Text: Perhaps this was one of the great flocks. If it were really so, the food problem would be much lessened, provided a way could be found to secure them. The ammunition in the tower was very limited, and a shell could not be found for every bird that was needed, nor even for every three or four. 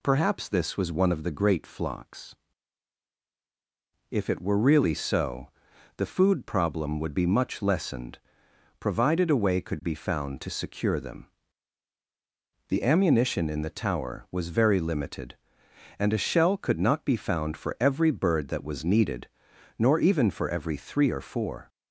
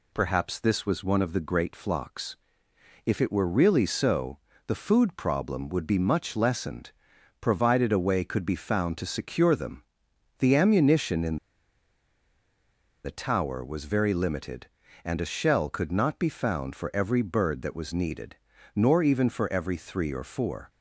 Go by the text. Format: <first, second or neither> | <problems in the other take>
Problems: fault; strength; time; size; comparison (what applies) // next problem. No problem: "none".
first | pauses between "in" and "the"; strong; at 11.3 s; 1.6 s long